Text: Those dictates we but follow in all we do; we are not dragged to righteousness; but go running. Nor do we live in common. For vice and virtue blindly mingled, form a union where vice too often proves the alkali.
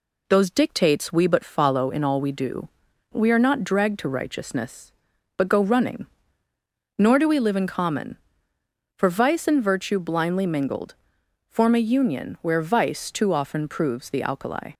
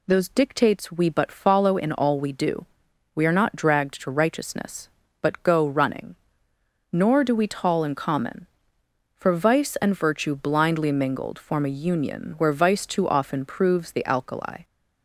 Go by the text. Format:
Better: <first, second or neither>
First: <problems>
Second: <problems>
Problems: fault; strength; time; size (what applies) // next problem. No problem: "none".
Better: first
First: none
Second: says "tall" for "live"; at 7.4 s